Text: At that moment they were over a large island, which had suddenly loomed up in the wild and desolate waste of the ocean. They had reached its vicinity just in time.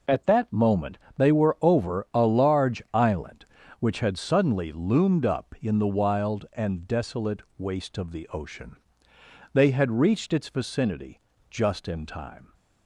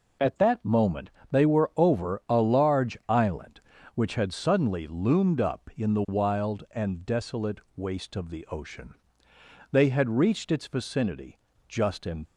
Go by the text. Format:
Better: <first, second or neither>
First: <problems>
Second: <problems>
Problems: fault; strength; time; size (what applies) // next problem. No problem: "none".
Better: first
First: pauses between "moment" and "they"; slight; at 0.9 s; 0.18 s long // pauses between "desolate" and "waste"; slight; at 7.4 s; 0.16 s long // pauses between "vicinity" and "just"; slight; at 11.1 s; 0.30 s long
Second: pauses between "moment" and "they"; slight; at 1.1 s; 0.20 s long // pauses between "desolate" and "waste"; slight; at 7.5 s; 0.16 s long // pauses between "vicinity" and "just"; slight; at 11.3 s; 0.30 s long // stops before "time"; at 12.2 s